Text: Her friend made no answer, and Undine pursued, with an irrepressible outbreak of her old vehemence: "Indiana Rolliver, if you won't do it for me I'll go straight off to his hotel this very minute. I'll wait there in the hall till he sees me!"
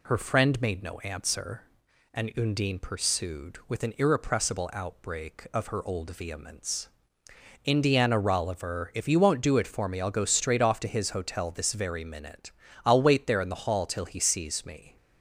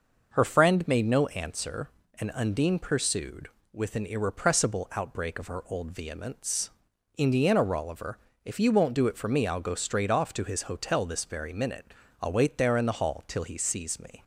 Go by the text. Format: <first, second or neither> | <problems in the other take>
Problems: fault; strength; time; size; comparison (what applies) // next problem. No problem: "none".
neither | none